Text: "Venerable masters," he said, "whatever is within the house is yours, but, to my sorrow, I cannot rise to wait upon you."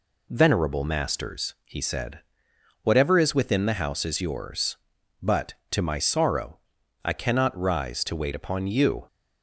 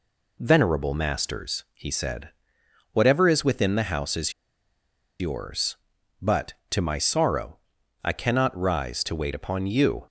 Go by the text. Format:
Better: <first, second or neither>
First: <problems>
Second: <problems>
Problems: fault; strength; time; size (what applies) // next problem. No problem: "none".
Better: first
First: none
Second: pauses between "is" and "yours"; noticeable; at 4.3 s; 0.88 s long